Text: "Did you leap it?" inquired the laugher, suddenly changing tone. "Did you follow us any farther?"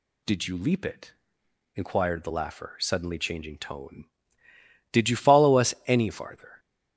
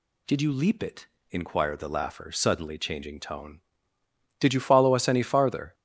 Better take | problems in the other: neither | none

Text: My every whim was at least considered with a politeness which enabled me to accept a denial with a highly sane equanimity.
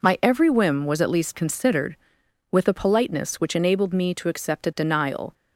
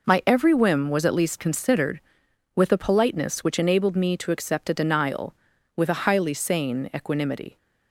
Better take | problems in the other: second | stops before "with a highly sane equanimity"; at 5.3 s

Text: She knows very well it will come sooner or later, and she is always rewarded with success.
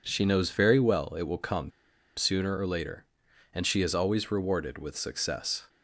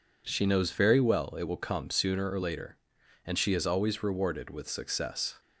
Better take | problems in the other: second | pauses between "come" and "sooner"; at 1.7 s; 0.45 s long

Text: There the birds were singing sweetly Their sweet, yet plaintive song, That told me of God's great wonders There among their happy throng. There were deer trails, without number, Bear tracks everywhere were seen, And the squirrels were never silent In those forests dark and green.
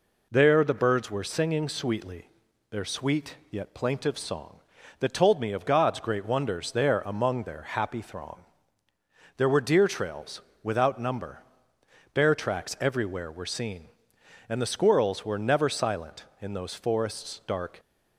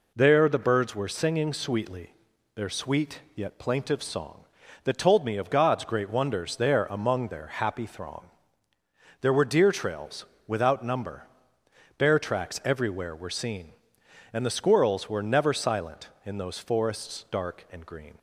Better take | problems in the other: second | pauses between "sweetly" and "Their"; at 2.2 s; 0.42 s long; also in the second // stops before "and green"; at 17.8 s

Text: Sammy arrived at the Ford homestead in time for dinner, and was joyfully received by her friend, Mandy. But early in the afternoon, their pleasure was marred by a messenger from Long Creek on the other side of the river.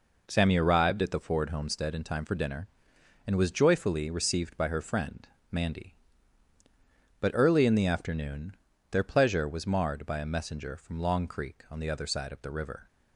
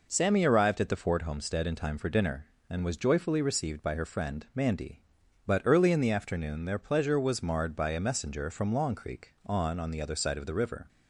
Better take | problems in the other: first | says "on" twice; at 9.7 s

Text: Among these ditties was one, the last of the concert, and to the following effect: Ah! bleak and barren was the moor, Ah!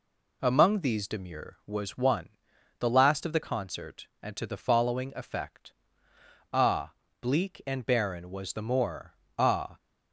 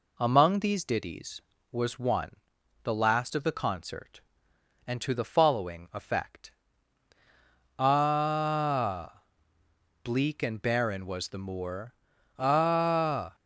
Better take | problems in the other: second | says "demure" for "ditties"; at 1.0 s

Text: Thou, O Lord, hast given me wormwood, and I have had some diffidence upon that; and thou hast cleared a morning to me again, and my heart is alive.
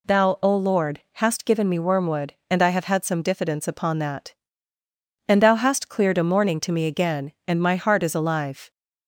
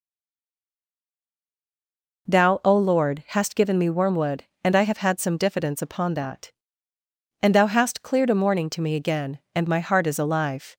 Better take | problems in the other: first | stays silent before the first word; until 2.2 s; 2.2 s long

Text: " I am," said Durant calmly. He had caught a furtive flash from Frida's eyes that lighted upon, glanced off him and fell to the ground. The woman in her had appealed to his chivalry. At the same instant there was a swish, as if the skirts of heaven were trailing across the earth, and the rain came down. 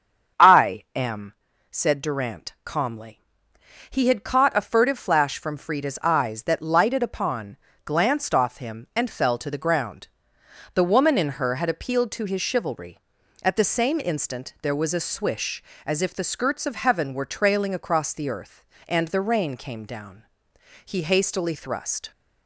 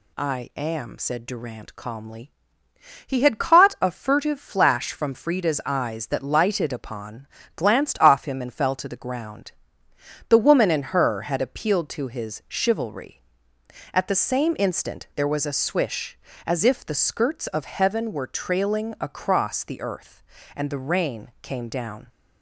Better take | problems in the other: second | starts louder than the rest; strong; until 1.8 s; 7.5 dB // goes on to say "He hastily thrust"; noticeable; from 20.8 s on; 1.2 s long

